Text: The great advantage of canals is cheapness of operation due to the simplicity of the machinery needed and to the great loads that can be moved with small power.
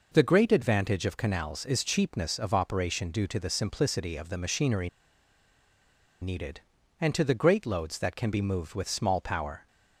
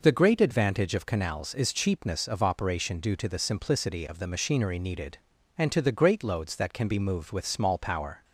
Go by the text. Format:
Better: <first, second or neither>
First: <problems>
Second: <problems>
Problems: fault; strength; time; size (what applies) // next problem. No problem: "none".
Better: second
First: pauses between "machinery" and "needed"; strong; at 4.8 s; 1.3 s long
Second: none